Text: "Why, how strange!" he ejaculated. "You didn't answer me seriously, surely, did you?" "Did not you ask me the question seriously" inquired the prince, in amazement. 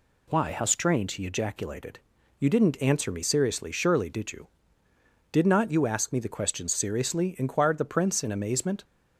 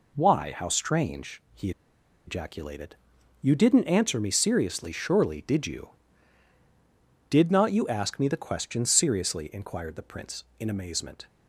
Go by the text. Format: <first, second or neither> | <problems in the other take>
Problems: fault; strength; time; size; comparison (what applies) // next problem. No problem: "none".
first | pauses between "he" and "ejaculated"; noticeable; at 1.7 s; 0.56 s long